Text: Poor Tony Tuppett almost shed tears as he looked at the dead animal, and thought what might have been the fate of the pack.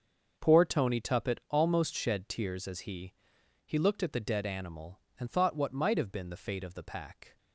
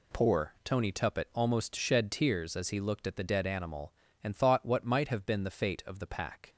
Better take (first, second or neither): second